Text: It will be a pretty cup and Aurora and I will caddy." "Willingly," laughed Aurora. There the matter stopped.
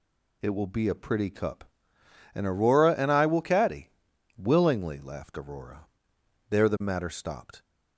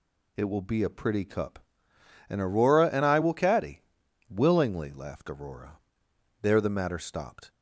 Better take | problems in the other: neither | none

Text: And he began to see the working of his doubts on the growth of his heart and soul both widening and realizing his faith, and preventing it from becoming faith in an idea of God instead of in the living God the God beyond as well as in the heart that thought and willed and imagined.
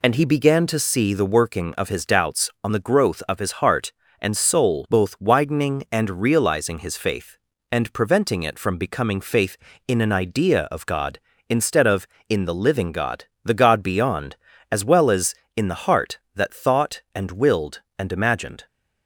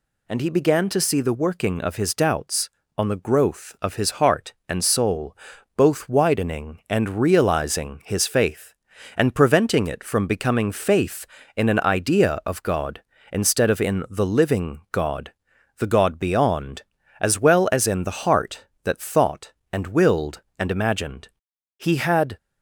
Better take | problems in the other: first | pauses between "soul" and "both"; at 5.3 s; 0.40 s long // pauses between "God" and "the"; noticeable; at 15.3 s; 0.48 s long; slight in the first // goes on to say "He had"; from 21.7 s on; 0.60 s long

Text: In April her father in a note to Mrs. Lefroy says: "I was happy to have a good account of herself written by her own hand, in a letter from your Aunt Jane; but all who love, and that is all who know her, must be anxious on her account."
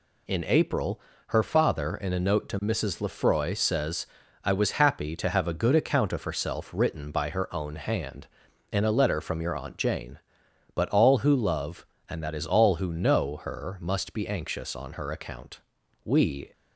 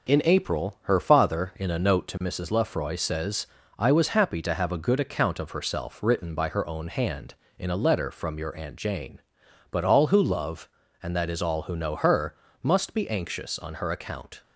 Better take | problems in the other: second | pauses between "April" and "her"; slight; at 1.0 s; 0.28 s long // goes on to say "We"; slight; from 16.0 s on; 0.48 s long

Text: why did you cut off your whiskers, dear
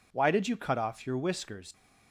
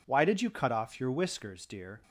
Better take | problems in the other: second | stops before "dear"; at 1.7 s

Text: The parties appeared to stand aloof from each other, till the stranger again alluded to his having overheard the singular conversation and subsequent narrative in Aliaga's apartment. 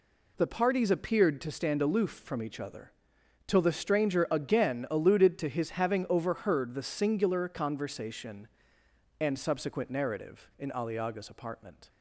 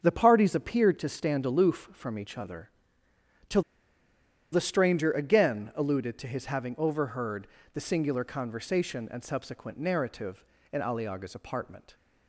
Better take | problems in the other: first | starts louder than the rest; until 1.0 s; 6.5 dB // pauses between "till" and "the"; noticeable; at 3.6 s; 0.90 s long // pauses between "overheard" and "the"; slight; at 7.4 s; 0.28 s long

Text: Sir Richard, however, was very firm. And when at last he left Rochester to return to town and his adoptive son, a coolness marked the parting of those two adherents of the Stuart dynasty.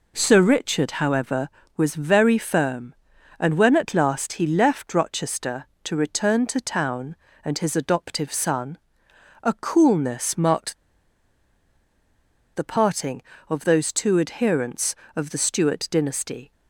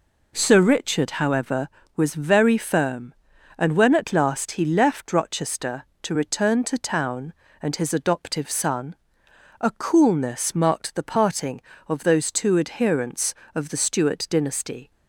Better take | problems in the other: second | pauses between "marked" and "the"; strong; at 10.7 s; 1.7 s long

